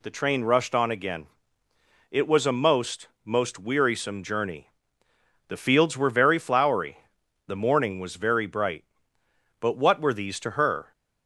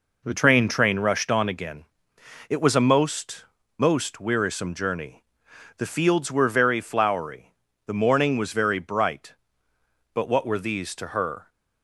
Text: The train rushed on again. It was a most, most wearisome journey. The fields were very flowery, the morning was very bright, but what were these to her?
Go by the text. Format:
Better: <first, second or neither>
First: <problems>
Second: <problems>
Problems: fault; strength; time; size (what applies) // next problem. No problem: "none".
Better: first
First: none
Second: says "train" twice; at 0.6 s